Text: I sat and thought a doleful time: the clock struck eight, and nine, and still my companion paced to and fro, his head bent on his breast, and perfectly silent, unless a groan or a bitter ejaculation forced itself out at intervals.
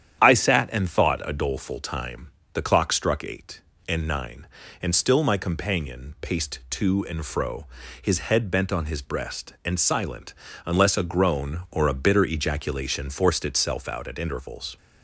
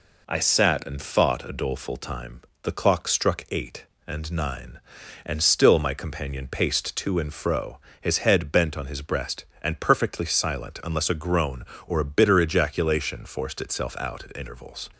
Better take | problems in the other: second | starts louder than the rest; strong; until 1.2 s; 9.5 dB // skips "perfectly"; at 9.7 s

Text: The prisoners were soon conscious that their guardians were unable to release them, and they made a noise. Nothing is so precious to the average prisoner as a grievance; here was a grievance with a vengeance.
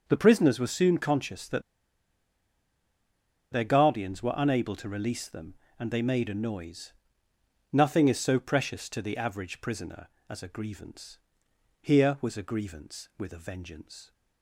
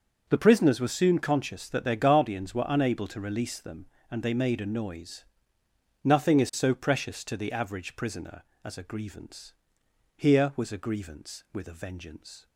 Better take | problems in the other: second | starts louder than the rest; until 1.0 s; 6 dB; also in the second // pauses between "that" and "their"; strong; at 1.6 s; 1.9 s long

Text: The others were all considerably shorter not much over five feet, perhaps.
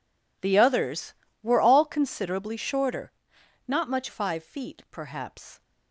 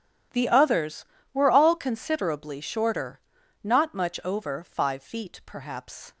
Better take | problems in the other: second | pauses between "shorter" and "not"; noticeable; at 3.1 s; 0.56 s long; also in the second // skips "over"; at 4.0 s

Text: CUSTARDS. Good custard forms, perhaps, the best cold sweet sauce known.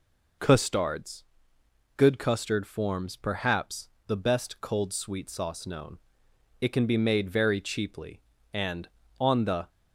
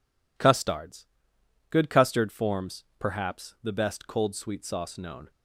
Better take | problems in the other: second | goes on to say "It can be made very cheaply and on the"; strong; from 6.6 s on; 3.0 s long

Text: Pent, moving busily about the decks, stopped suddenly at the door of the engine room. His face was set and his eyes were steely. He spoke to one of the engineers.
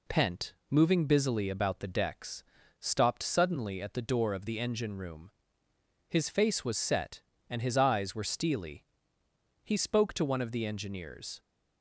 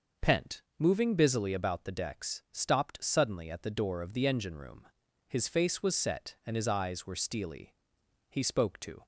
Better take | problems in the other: first | stops before "one of the engineers"; at 9.0 s

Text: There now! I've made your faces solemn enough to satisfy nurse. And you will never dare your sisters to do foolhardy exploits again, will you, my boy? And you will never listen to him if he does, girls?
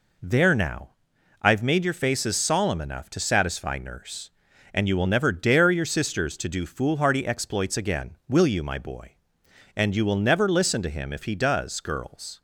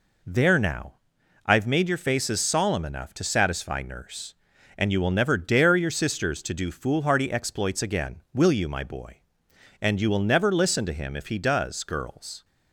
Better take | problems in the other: neither | none

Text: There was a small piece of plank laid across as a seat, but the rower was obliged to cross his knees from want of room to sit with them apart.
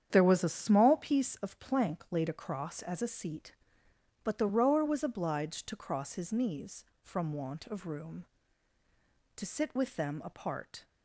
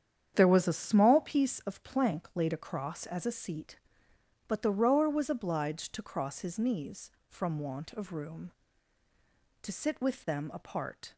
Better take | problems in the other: neither | starts louder than the rest; strong; the same in both

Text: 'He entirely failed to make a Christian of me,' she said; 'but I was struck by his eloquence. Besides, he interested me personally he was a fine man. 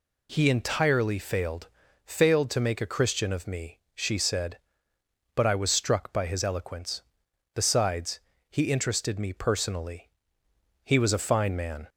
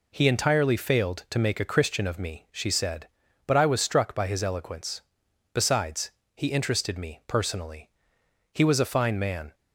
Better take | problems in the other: second | says "failed" twice; at 2.0 s // pauses between "personally" and "he"; noticeable; at 10.0 s; 0.76 s long; noticeable in the second

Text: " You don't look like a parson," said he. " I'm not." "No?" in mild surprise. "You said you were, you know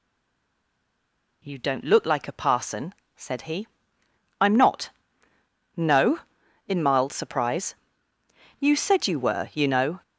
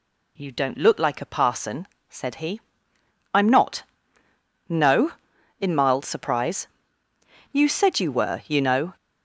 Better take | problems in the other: second | stays silent before the first word; noticeable; until 1.4 s; 1.4 s long

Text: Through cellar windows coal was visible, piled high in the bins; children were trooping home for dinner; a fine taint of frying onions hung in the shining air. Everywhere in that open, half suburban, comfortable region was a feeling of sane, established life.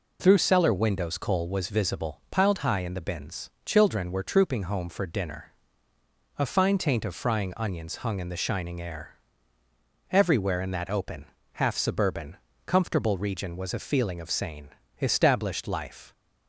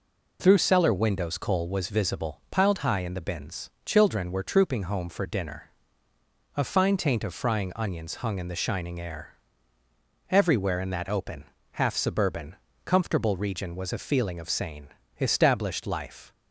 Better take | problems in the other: neither | none

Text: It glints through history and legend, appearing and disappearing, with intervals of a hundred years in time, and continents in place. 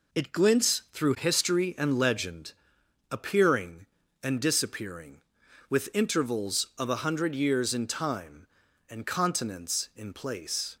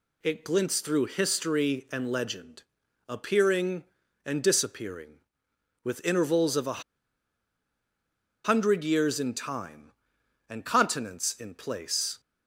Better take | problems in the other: first | pauses between "a" and "hundred"; strong; at 6.8 s; 1.6 s long

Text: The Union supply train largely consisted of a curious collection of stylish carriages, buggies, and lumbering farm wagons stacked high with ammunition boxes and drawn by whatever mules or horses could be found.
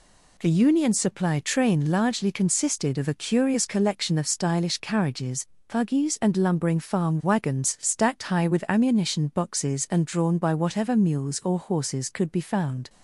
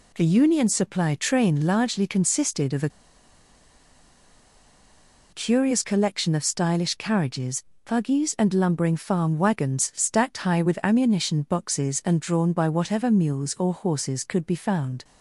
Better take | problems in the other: first | pauses between "a" and "curious"; strong; at 2.9 s; 2.4 s long

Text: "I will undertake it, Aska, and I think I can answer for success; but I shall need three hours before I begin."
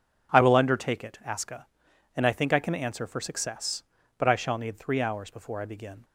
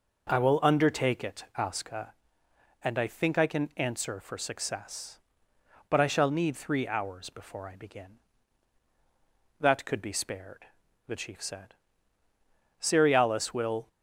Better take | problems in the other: first | goes on to say "That could be spared the chief said Cerealis will"; strong; from 9.5 s on; 4.2 s long

